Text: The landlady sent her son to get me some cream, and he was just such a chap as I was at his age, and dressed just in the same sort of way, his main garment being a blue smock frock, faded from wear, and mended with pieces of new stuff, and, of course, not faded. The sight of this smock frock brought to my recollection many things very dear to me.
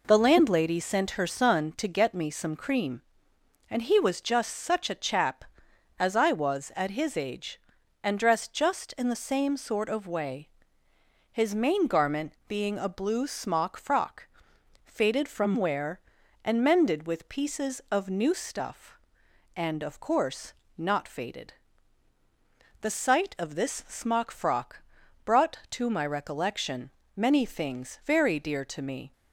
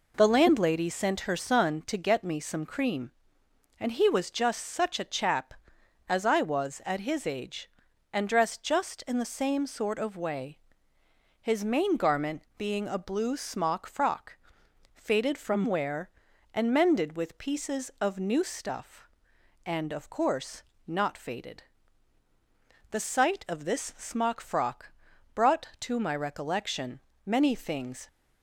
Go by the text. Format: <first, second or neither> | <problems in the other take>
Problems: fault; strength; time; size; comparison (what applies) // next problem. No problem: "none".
first | pauses between "frock" and "brought"; at 24.9 s; 0.42 s long; also in the first // pauses between "recollection" and "many"; slight; at 27.0 s; 0.24 s long; slight in the first // stops before "very dear to me"; at 28.0 s